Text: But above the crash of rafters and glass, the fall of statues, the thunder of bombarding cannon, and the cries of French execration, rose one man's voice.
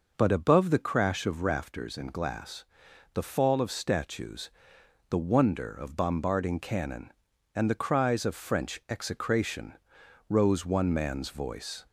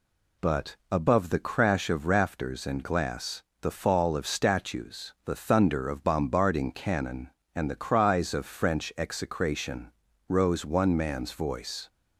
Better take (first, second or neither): second